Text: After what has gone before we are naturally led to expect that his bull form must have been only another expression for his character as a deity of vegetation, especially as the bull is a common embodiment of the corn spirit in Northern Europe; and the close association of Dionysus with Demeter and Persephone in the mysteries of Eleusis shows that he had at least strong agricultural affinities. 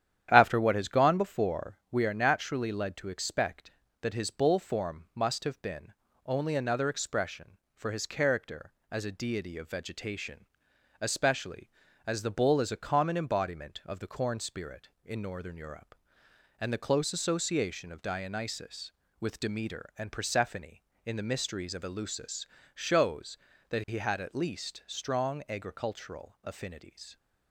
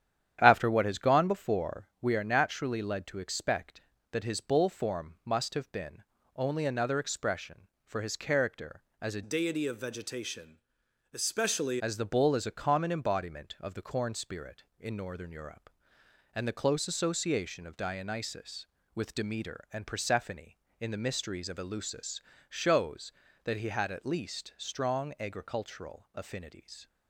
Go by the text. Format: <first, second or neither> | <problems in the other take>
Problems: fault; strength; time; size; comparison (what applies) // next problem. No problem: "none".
first | starts louder than the rest; strong; until 1.4 s; 10 dB; strong in the first // pauses between "been" and "only"; slight; at 6.0 s; 0.30 s long; slight in the first // changes voice from "deity" to "especially"; from 9.2 to 11.7 s; 2.5 s long // pauses between "Eleusis" and "shows"; slight; at 22.2 s; 0.30 s long; slight in the first